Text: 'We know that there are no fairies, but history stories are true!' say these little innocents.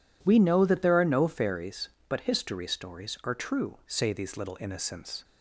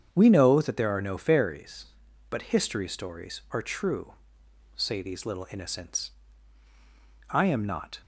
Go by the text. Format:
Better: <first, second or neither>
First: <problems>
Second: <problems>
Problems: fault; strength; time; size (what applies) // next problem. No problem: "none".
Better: first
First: none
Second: starts louder than the rest; strong; until 1.1 s; 7.5 dB // goes on to say "I am not"; noticeable; from 7.2 s on; 0.72 s long